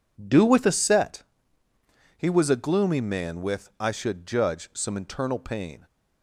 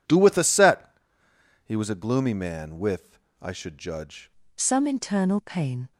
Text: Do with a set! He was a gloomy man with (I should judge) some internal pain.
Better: first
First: none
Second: changes voice at "some"; from 4.5 s on; 1.4 s long

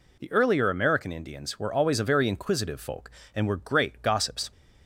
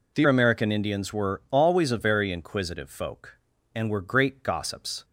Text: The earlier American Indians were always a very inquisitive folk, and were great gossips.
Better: first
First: none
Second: skips "earlier"; at 0.2 s

